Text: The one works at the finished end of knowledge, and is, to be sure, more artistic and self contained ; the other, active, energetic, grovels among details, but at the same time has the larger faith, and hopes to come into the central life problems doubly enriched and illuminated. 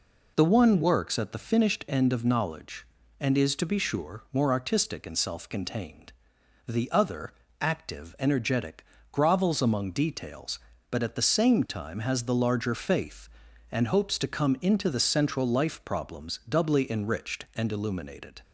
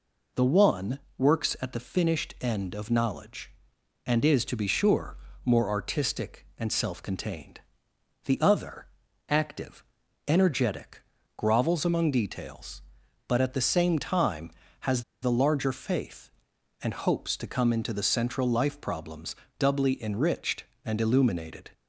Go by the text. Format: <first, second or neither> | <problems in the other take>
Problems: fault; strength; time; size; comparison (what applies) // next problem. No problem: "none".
first | pauses between "one" and "works"; slight; at 0.9 s; 0.18 s long // pauses between "has" and "the"; slight; at 15.0 s; 0.19 s long // pauses between "problems" and "doubly"; slight; at 19.3 s; 0.22 s long